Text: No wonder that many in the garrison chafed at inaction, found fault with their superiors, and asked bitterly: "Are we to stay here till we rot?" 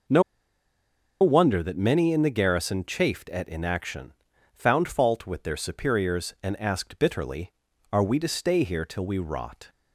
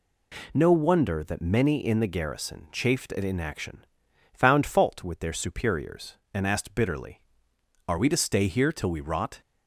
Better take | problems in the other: second | pauses between "No" and "wonder"; at 0.2 s; 0.98 s long

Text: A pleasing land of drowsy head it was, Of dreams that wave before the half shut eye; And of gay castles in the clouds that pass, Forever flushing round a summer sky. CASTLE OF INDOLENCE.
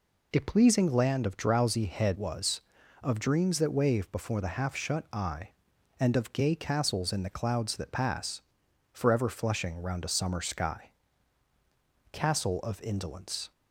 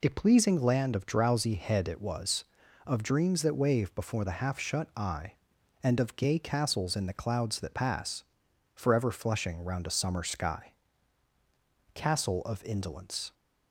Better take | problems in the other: second | skips "it"; at 2.1 s

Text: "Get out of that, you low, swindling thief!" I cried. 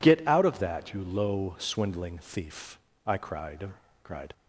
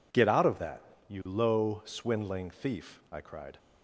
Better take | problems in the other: second | says "cried" twice; at 4.0 s

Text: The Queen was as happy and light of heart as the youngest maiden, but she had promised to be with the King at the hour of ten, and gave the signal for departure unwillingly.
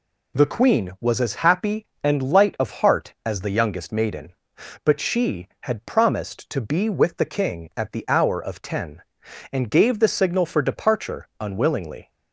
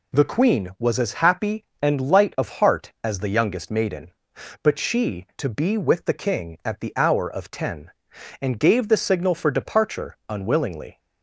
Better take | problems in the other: first | skips "had promised"; at 5.3 s

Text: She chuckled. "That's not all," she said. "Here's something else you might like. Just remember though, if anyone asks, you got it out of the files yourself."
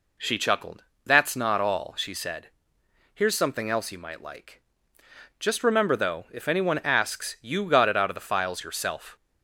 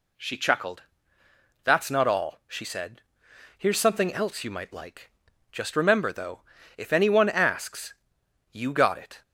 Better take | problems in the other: first | stops before "out of the files yourself"; at 9.2 s

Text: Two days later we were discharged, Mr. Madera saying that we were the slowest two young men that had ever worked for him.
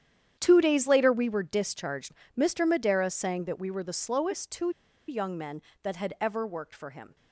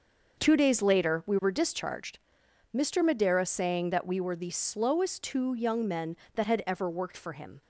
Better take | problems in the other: second | starts louder than the rest; strong; until 1.4 s; 9.5 dB; also in the second // pauses between "two" and "young"; at 4.6 s; 0.38 s long

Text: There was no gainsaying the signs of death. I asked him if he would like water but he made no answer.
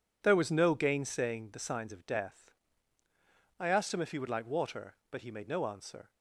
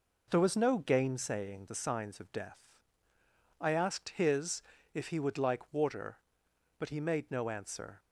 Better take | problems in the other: first | says "his" for "him"; at 4.1 s

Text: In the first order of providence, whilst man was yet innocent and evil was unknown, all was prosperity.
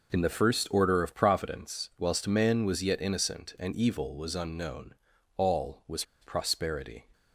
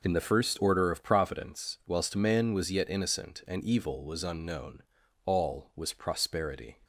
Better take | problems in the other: second | pauses between "was" and "prosperity"; slight; at 6.0 s; 0.18 s long

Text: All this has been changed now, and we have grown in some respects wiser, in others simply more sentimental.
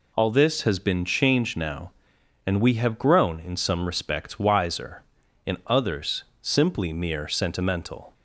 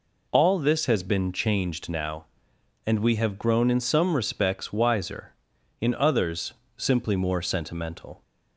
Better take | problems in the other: second | pauses between "others" and "simply"; slight; at 6.2 s; 0.16 s long; slight in the second // says "mere" for "more"; at 6.9 s

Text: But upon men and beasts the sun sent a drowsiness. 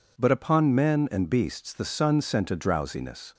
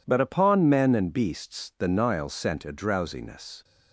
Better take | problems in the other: first | says "nile" for "sun"; at 1.8 s

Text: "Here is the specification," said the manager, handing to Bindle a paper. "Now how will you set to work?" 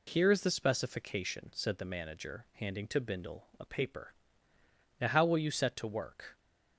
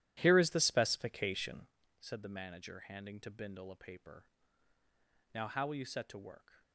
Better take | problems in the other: first | starts louder than the rest; strong; until 1.7 s; 12 dB

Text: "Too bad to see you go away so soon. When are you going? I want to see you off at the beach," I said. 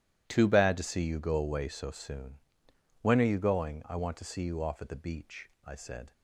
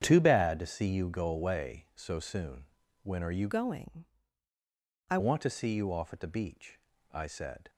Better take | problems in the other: first | starts louder than the rest; strong; until 1.0 s; 8.5 dB // changes voice from "going" to "I"; from 3.5 to 5.1 s; 1.6 s long

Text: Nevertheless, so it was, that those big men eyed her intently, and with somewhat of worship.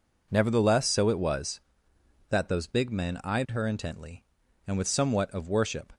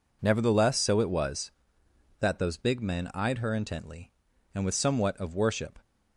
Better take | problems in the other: neither | none

